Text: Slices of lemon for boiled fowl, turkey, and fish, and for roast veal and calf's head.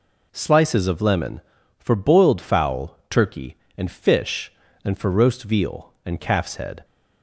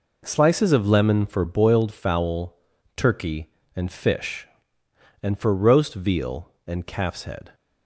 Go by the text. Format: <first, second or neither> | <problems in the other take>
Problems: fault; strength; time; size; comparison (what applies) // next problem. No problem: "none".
neither | none